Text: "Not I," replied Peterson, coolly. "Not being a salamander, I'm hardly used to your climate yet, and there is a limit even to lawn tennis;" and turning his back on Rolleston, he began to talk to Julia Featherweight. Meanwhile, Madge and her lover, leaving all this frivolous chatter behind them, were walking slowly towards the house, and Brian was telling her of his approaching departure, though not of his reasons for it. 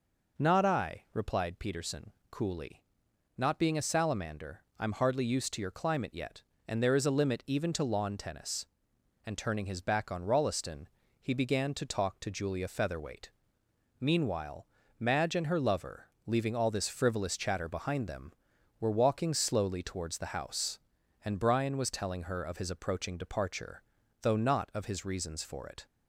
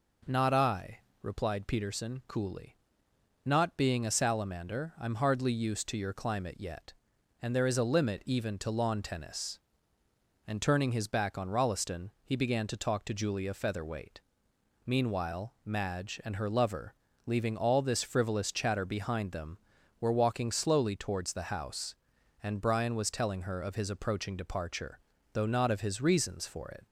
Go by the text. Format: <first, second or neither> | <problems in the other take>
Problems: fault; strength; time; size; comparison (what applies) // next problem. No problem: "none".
neither | none